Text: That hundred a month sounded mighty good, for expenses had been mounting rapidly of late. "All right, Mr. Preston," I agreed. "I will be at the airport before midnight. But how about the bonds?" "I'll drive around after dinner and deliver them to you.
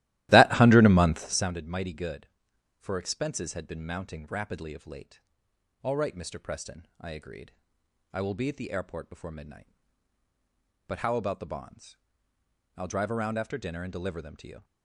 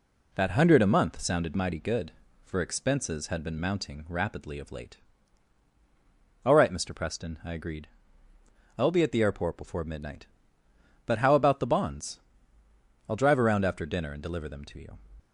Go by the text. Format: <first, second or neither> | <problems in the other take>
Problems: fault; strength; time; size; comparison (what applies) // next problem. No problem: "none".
second | starts louder than the rest; strong; until 1.5 s; 15.5 dB